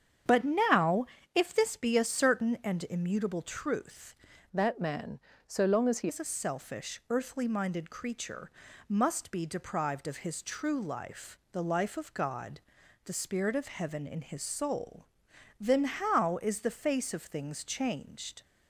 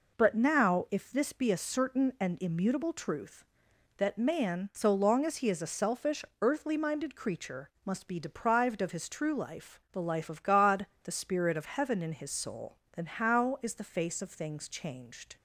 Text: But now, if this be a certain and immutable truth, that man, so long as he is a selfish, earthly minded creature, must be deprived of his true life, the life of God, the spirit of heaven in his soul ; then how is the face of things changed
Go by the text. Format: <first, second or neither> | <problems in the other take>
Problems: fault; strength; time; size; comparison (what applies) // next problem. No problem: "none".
second | starts louder than the rest; strong; until 1.5 s; 8 dB // changes voice from "that" to "he"; from 4.5 to 6.0 s; 1.5 s long